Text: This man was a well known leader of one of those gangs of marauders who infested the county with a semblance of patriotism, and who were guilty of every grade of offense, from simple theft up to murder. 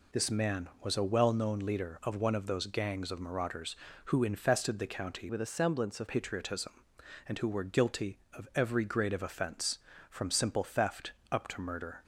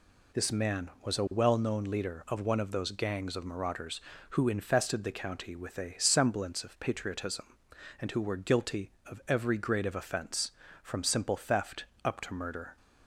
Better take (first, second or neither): second